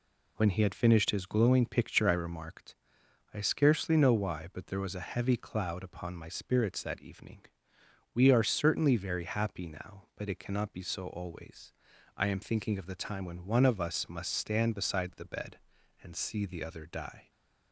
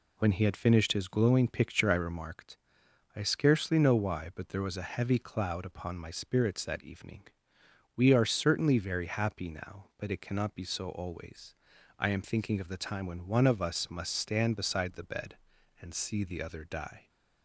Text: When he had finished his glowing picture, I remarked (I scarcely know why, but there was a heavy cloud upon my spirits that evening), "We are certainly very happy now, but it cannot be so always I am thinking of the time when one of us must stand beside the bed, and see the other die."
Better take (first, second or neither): neither